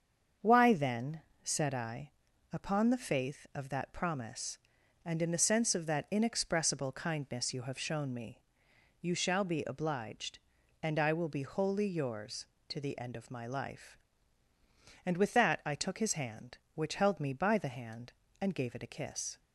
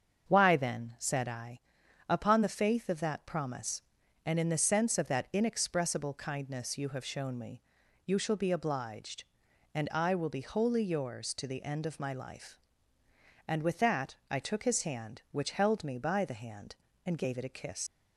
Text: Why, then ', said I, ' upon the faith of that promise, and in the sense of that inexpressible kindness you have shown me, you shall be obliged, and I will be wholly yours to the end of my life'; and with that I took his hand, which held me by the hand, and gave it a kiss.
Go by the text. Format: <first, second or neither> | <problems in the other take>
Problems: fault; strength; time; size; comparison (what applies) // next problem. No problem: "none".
first | starts louder than the rest; strong; until 1.3 s; 7.5 dB; also in the first // leaves "kiss" unfinished; at 17.8 s; 90 ms